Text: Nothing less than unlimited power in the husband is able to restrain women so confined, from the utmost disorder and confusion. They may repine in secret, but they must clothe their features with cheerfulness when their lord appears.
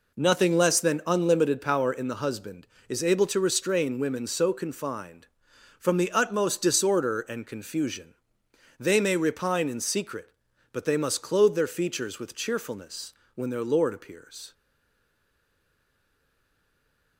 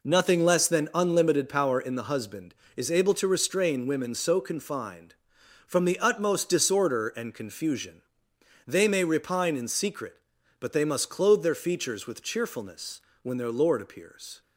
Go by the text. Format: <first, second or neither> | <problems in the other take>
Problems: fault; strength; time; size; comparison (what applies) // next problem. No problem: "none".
second | pauses between "cheerfulness" and "when"; slight; at 13.1 s; 0.20 s long; slight in the second // stays silent after the last word; strong; from 14.5 s on; 2.6 s long